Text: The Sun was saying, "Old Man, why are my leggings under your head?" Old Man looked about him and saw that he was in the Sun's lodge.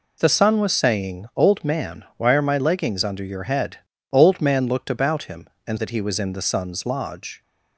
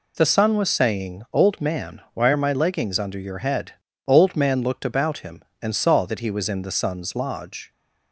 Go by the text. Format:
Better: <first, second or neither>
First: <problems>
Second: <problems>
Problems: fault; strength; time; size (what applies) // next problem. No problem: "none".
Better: second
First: skips "saw"; at 5.7 s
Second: none